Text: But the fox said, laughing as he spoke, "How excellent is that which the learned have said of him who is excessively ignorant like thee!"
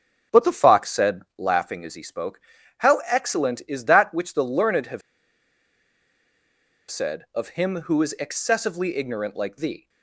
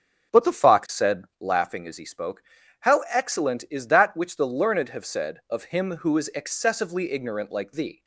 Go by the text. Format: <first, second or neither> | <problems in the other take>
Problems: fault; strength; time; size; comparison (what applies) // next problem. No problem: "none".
second | starts louder than the rest; strong; until 1.4 s; 8 dB; strong in the second // pauses between "have" and "said"; strong; at 5.0 s; 1.8 s long